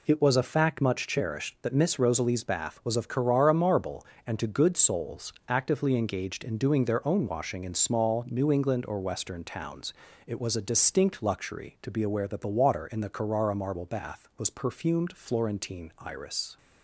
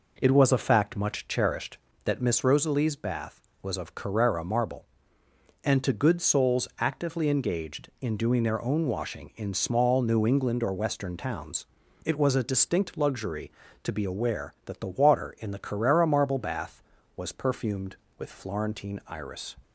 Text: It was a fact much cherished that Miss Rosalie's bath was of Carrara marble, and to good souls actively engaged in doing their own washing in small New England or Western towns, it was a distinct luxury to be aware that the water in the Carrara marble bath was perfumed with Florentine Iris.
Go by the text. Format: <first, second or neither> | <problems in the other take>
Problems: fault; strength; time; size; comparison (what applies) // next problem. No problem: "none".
second | pauses between "souls" and "actively"; slight; at 5.3 s; 0.16 s long // skips "with"; at 15.1 s